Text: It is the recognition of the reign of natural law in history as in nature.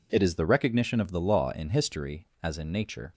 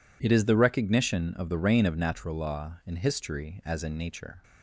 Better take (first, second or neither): second